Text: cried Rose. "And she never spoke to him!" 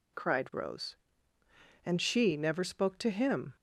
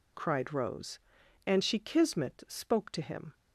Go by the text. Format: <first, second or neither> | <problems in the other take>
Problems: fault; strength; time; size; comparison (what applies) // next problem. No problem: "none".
first | says "kismet" for "never"; at 1.7 s